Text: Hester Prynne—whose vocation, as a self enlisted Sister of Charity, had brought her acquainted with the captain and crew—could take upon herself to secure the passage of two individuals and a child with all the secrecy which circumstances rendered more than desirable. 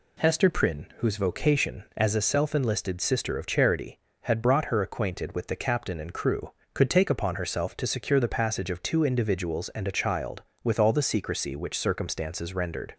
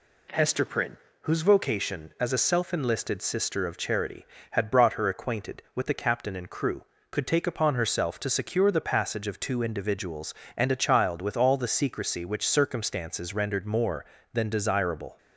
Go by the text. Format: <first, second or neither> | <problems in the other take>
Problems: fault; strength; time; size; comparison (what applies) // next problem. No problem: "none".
second | stops before "more than desirable"; at 12.9 s